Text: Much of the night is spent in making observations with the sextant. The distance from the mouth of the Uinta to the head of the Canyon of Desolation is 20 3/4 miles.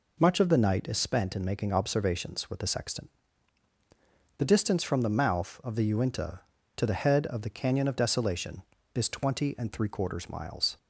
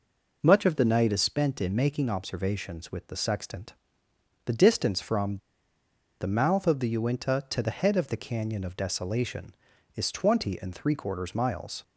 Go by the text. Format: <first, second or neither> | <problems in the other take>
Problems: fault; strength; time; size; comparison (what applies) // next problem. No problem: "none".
first | pauses between "from" and "the"; noticeable; at 5.3 s; 0.83 s long